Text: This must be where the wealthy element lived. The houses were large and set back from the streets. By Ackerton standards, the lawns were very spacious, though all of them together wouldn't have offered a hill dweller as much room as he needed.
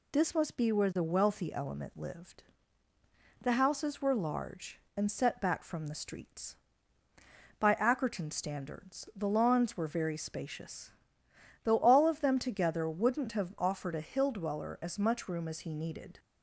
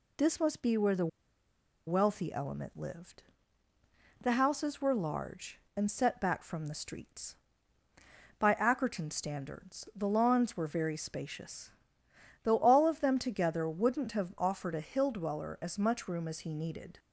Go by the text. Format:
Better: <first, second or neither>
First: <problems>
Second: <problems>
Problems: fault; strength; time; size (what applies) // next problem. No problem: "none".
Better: first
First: none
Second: pauses between "the" and "wealthy"; noticeable; at 1.0 s; 0.79 s long